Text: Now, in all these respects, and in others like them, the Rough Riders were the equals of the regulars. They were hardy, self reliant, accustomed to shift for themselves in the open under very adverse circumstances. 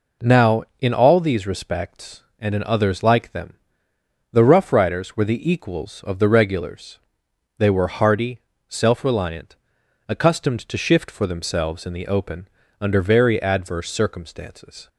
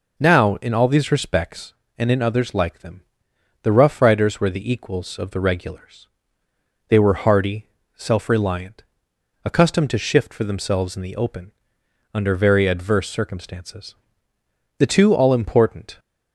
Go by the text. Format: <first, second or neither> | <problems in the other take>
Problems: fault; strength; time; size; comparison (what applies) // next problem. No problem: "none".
first | pauses between "open" and "under"; noticeable; at 11.5 s; 0.64 s long; slight in the first // goes on to say "The two all important"; noticeable; from 14.7 s on; 1.2 s long